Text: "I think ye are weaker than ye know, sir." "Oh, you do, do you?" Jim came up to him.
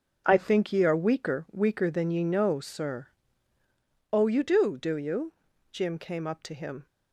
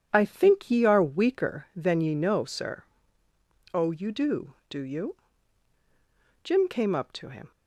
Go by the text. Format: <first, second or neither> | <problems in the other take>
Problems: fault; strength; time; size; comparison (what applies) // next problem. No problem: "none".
second | starts louder than the rest; until 1.2 s; 6.5 dB // says "weaker" twice; at 1.5 s